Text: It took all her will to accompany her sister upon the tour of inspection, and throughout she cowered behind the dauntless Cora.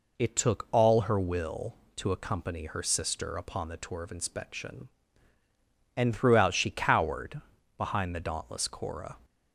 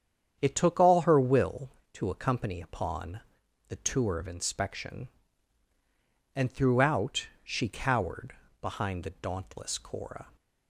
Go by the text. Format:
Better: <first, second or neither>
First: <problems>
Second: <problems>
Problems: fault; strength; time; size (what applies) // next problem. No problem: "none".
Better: first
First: pauses between "cowered" and "behind"; slight; at 7.4 s; 0.36 s long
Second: starts louder than the rest; strong; until 1.4 s; 8.5 dB // skips "her sister"; at 2.5 s // pauses between "upon" and "the"; noticeable; at 3.2 s; 0.48 s long // pauses between "cowered" and "behind"; slight; at 8.3 s; 0.26 s long